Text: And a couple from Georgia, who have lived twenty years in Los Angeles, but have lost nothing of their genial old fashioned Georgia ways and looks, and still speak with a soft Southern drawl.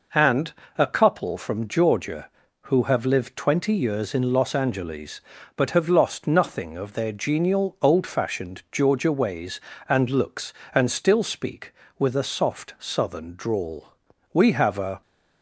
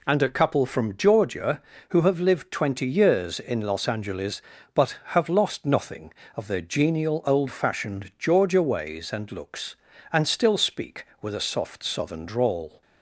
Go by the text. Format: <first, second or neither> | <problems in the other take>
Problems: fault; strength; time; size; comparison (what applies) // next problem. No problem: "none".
second | pauses between "And" and "a"; slight; at 0.5 s; 0.26 s long // goes on to say "We have a"; noticeable; from 14.3 s on; 0.68 s long